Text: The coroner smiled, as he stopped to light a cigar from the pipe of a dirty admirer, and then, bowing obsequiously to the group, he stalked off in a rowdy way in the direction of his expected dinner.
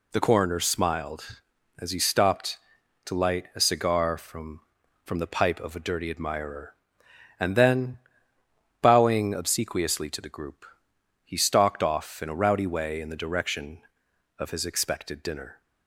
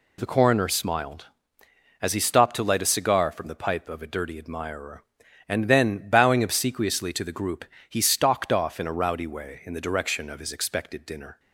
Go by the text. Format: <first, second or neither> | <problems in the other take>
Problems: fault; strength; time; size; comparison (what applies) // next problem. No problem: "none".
second | says "from" twice; at 5.0 s